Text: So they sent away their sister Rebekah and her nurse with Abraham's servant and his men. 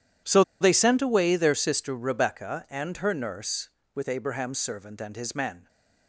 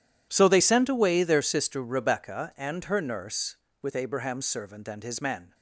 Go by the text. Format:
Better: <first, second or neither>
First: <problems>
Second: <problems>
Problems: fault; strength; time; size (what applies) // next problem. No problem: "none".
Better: second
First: pauses between "So" and "they"; slight; at 0.4 s; 0.19 s long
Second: none